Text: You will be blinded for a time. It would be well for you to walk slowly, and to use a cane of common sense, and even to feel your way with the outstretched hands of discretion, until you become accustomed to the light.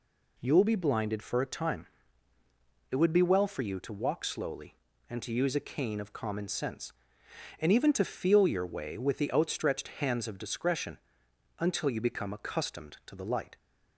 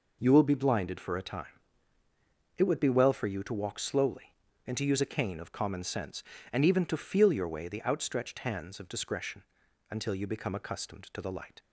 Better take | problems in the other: first | skips "with"; at 7.6 s

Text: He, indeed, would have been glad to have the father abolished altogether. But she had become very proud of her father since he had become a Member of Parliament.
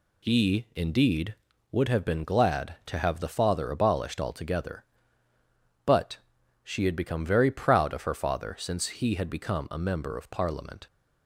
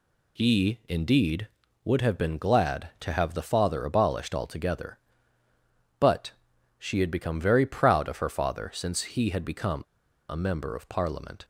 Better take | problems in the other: first | pauses between "But" and "she"; noticeable; at 6.3 s; 0.46 s long; also in the first // pauses between "become" and "a"; noticeable; at 9.8 s; 0.47 s long

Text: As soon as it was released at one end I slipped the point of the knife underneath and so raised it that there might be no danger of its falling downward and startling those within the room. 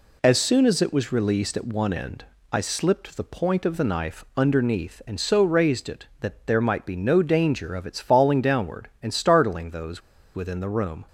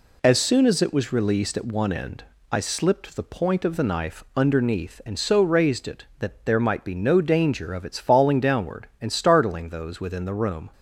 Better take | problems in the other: second | pauses between "end" and "I"; slight; at 2.2 s; 0.26 s long; slight in the second // pauses between "those" and "within"; slight; at 10.0 s; 0.34 s long

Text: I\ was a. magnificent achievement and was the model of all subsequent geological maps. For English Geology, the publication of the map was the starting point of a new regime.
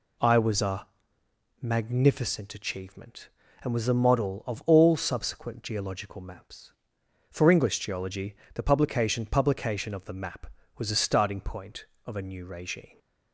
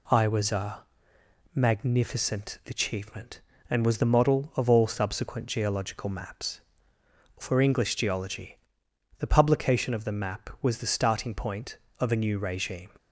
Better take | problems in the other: second | says "publication" twice; at 9.2 s

